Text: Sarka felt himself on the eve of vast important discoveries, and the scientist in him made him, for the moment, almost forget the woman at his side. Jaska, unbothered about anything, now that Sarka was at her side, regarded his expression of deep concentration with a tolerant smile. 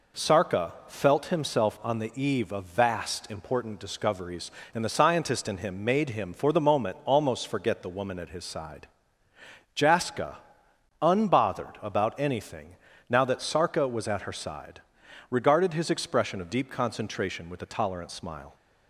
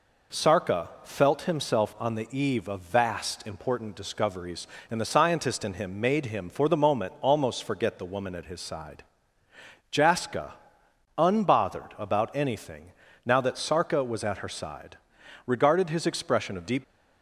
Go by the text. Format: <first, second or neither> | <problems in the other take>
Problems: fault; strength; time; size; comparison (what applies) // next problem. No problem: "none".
first | pauses between "Sarka" and "felt"; slight; at 0.8 s; 0.16 s long; slight in the first // stops before "concentration with a tolerant smile"; at 16.8 s